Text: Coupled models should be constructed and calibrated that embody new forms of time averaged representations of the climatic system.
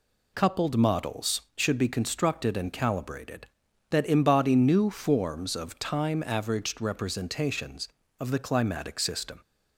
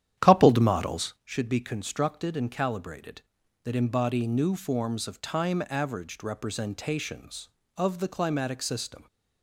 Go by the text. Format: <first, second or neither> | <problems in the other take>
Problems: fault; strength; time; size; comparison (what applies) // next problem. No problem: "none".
first | starts louder than the rest; strong; until 1.2 s; 10.5 dB